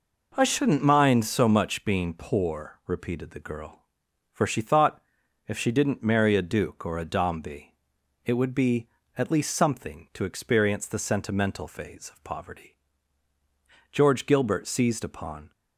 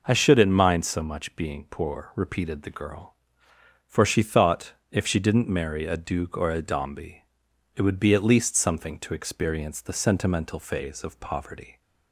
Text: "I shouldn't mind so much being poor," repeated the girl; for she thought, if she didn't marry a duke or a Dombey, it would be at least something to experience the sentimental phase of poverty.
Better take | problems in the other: second | goes on to say "George Gilbert seized upon"; from 13.9 s on; 1.6 s long

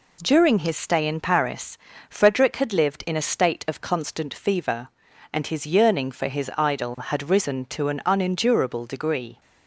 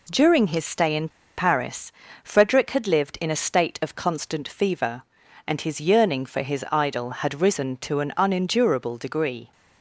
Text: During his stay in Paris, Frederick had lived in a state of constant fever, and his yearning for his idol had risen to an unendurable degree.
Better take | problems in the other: first | pauses between "in" and "Paris"; slight; at 1.0 s; 0.27 s long

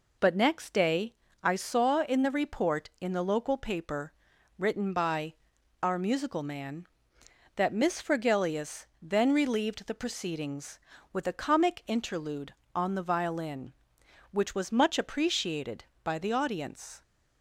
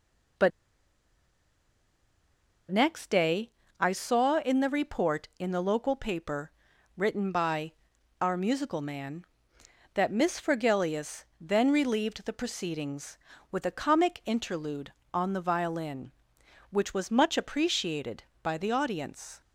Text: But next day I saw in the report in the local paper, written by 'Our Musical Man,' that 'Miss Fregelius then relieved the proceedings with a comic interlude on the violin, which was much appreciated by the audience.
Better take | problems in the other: first | pauses between "But" and "next"; strong; at 0.5 s; 2.2 s long // pauses between "day" and "I"; slight; at 3.5 s; 0.30 s long; slight in the first // pauses between "by" and "Our"; noticeable; at 7.7 s; 0.48 s long; noticeable in the first // pauses between "Fregelius" and "then"; slight; at 11.2 s; 0.16 s long; slight in the first

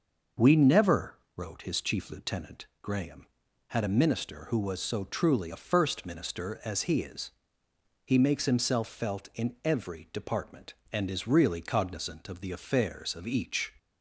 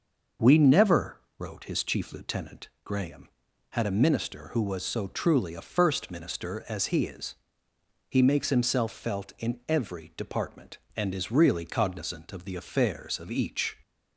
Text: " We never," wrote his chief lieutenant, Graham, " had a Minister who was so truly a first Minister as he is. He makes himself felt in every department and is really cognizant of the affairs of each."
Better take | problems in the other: neither | none

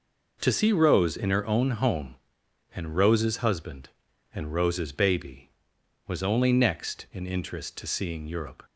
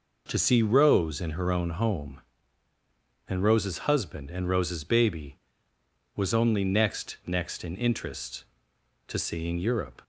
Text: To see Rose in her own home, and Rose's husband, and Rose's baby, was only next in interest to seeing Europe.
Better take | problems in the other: first | says "next" twice; at 7.2 s

